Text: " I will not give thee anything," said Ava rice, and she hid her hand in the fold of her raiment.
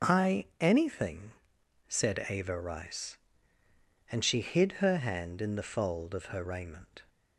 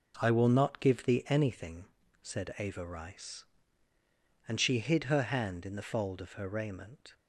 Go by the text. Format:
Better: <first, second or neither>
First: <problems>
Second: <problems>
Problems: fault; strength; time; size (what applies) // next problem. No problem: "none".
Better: second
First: starts louder than the rest; until 1.1 s; 6.5 dB // skips "will not give thee"; at 0.5 s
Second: none